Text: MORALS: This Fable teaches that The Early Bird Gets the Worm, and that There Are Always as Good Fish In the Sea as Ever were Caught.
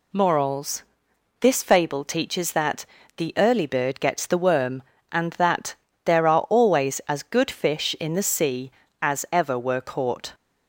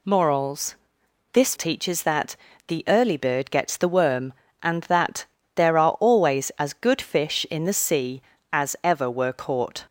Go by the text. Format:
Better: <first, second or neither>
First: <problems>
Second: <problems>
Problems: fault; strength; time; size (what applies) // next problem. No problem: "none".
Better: first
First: pauses between "that" and "The"; slight; at 2.8 s; 0.32 s long // pauses between "that" and "There"; slight; at 5.7 s; 0.30 s long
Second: skips "Fable"; at 1.5 s // pauses between "that" and "The"; slight; at 2.3 s; 0.32 s long // pauses between "that" and "There"; slight; at 5.2 s; 0.30 s long